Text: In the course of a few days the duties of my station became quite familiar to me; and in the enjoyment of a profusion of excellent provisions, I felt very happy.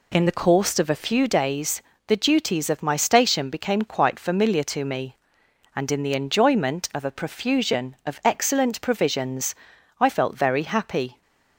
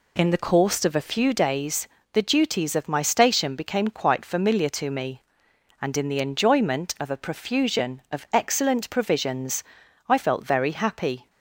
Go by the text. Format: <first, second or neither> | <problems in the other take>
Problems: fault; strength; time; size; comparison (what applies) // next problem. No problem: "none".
neither | pauses between "days" and "the"; slight; the same in both